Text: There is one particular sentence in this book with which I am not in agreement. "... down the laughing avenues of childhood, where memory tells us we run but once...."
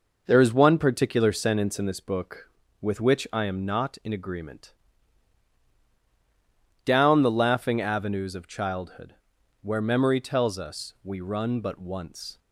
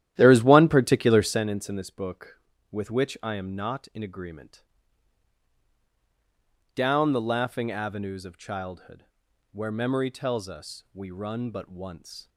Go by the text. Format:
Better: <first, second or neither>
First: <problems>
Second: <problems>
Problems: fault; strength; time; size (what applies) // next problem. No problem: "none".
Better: first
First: none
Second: starts louder than the rest; strong; until 1.4 s; 12.5 dB